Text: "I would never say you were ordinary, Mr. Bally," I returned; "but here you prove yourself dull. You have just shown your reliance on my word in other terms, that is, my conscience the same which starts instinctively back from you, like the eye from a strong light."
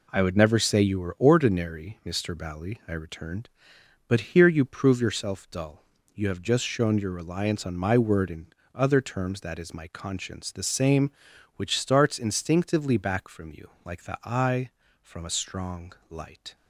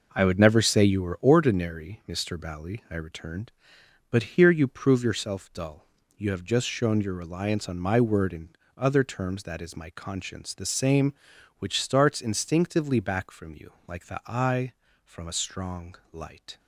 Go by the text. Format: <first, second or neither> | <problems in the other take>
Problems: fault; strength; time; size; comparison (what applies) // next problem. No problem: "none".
first | starts louder than the rest; noticeable; until 1.3 s; 5.5 dB // pauses between "in" and "other"; slight; at 8.4 s; 0.26 s long; slight in the first // pauses between "strong" and "light"; slight; at 15.9 s; 0.18 s long; slight in the first